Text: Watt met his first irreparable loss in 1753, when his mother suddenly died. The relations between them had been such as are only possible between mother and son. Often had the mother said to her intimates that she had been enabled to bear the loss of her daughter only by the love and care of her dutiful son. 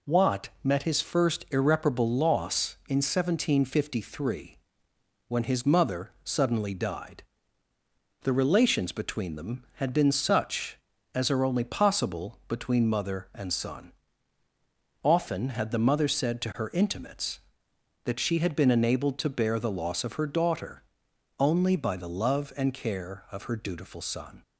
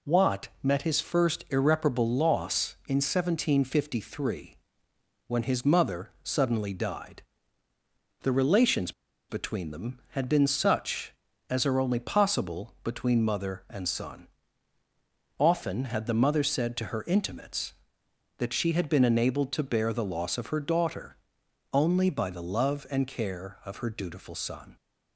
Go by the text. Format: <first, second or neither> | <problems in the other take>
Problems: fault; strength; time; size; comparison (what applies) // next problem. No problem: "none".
first | pauses between "relations" and "between"; at 8.9 s; 0.37 s long // pauses between "daughter" and "only"; noticeable; at 21.1 s; 0.56 s long; noticeable in the first